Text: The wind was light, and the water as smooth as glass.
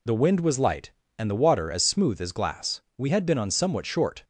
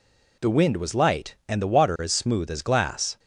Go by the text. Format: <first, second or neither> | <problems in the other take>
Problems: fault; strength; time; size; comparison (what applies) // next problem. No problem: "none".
second | goes on to say "We had been on somewhat short"; noticeable; from 2.9 s on; 1.2 s long